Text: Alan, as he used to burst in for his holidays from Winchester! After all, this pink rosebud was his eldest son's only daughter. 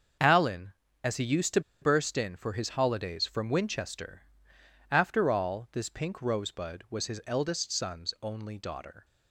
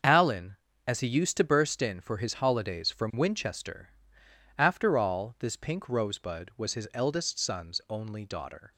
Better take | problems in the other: second | starts louder than the rest; until 1.5 s; 6.5 dB; also in the second // pauses between "to" and "burst"; slight; at 1.5 s; 0.21 s long

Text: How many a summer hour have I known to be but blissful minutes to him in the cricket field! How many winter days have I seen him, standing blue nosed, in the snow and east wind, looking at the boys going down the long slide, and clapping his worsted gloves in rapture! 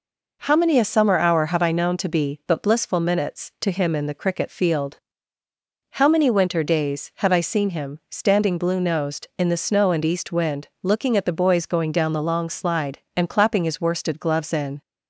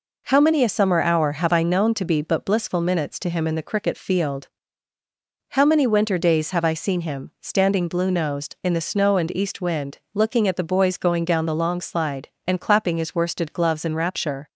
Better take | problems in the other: second | stops before "rapture"; at 14.8 s

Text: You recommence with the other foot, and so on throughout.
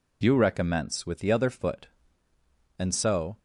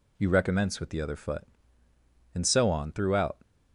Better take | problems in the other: second | stops before "on throughout"; at 3.3 s

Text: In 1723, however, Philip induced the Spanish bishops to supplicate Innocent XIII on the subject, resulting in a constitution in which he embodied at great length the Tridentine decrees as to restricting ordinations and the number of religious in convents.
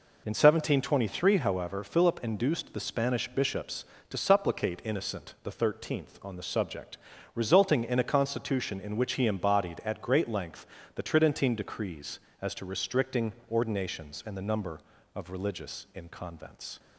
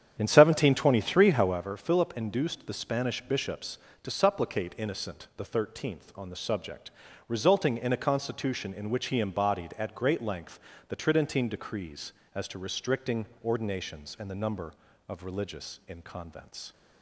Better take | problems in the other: first | starts louder than the rest; strong; until 1.7 s; 9 dB // pauses between "length" and "the"; slight; at 10.5 s; 0.30 s long; slight in the first // pauses between "restricting" and "ordinations"; slight; at 13.2 s; 0.18 s long; slight in the first

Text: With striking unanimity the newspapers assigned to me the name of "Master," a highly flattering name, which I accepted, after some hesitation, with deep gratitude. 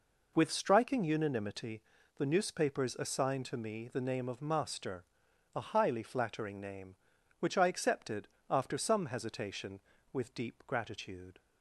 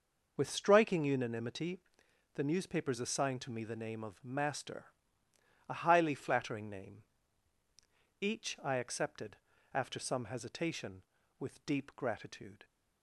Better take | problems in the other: first | pauses between "unanimity" and "the"; noticeable; at 1.7 s; 0.56 s long; slight in the first // says "each" for "which"; at 8.2 s

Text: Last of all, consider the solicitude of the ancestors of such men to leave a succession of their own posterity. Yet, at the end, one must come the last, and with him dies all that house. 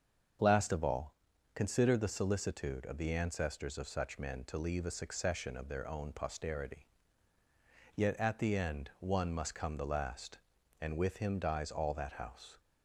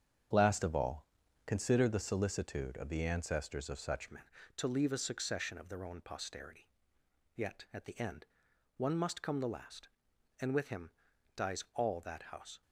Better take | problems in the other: first | starts louder than the rest; strong; until 1.7 s; 8 dB; also in the first // changes voice at "men"; from 4.0 s on; 8.6 s long // pauses between "him" and "dies"; at 10.9 s; 0.44 s long

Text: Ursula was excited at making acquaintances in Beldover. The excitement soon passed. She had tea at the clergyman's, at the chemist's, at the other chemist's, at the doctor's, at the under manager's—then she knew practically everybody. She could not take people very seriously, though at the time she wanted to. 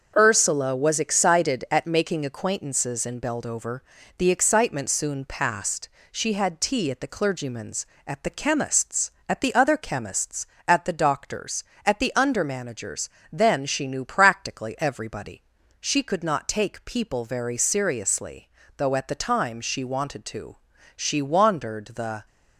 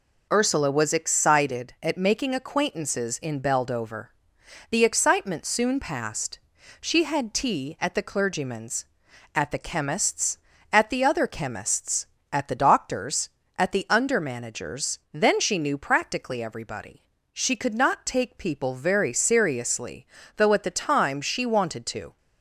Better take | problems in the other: second | starts louder than the rest; until 1.1 s; 6.5 dB // goes on to say "She wandered the"; noticeable; from 20.9 s on; 1.3 s long

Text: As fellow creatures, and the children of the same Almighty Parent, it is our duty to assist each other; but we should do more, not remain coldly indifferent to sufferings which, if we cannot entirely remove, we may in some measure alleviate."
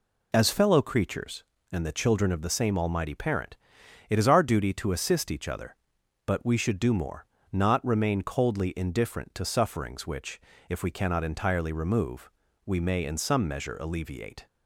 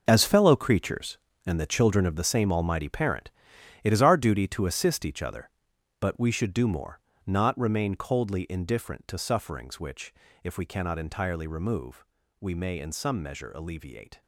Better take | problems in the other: first | gets quieter; strong; throughout; 12 dB

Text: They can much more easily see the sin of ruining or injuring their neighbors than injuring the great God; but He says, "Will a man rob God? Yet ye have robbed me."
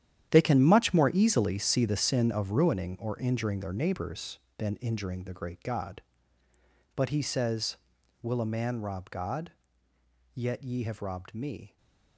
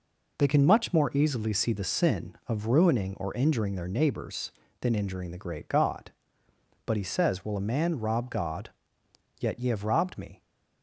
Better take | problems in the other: second | gets quieter; strong; throughout; 13.5 dB // stays silent after the last word; slight; from 11.6 s on; 0.5 s long

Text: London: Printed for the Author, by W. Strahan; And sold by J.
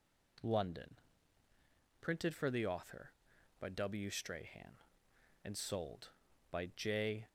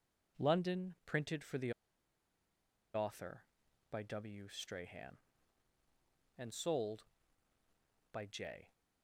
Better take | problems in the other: first | pauses between "the" and "Author"; at 1.7 s; 1.2 s long

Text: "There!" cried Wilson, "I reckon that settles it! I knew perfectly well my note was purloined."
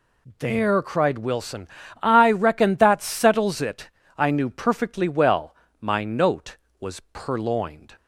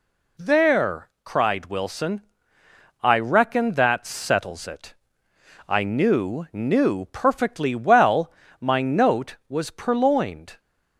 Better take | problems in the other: first | says "knew" twice; at 6.5 s // pauses between "well" and "my"; slight; at 8.3 s; 0.30 s long; slight in the first

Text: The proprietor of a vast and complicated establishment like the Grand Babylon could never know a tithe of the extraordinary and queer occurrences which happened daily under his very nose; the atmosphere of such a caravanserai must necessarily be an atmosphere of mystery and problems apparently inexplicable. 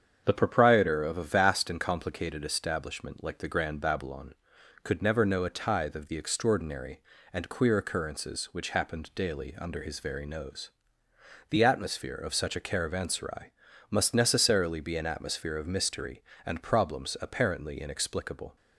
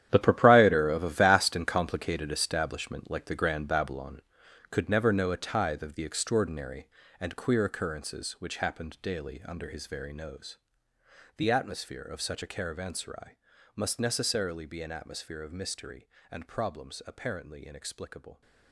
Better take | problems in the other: first | gets quieter; strong; throughout; 13.5 dB // starts louder than the rest; strong; until 1.1 s; 10.5 dB; strong in the first // pauses between "caravanserai" and "must"; at 13.3 s; 0.40 s long; also in the first

